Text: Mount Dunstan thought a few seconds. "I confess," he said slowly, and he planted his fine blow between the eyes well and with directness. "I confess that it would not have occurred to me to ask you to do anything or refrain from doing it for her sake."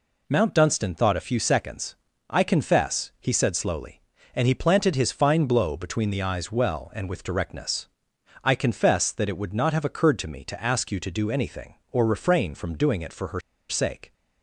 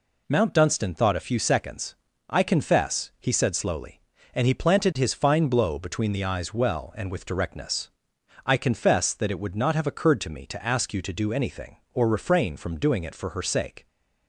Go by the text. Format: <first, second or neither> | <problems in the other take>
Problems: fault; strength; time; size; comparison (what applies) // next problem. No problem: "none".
second | pauses between "her" and "sake"; slight; at 13.4 s; 0.28 s long